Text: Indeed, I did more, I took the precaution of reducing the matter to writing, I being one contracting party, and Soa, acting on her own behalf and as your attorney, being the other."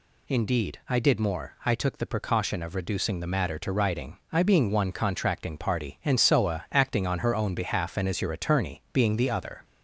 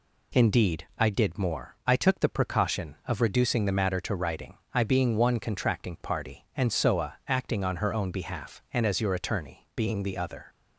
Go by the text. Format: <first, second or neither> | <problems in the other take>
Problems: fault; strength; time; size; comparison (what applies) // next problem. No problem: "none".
second | gets louder; slight; throughout; 2 dB